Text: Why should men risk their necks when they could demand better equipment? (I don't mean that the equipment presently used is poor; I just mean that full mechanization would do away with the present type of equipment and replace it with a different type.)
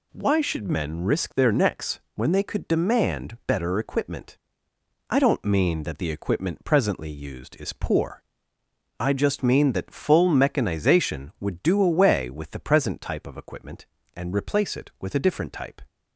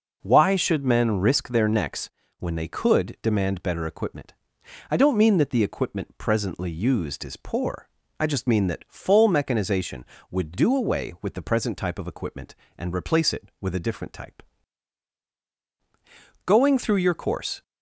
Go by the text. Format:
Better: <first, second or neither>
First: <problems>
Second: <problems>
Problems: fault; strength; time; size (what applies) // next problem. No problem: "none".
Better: first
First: pauses between "necks" and "when"; slight; at 1.9 s; 0.16 s long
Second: pauses between "necks" and "when"; slight; at 2.1 s; 0.30 s long // goes on to say "Going through your course"; noticeable; from 16.4 s on; 1.1 s long